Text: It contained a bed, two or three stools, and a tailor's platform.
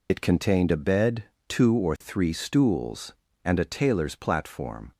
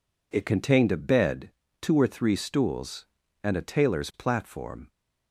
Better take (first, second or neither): second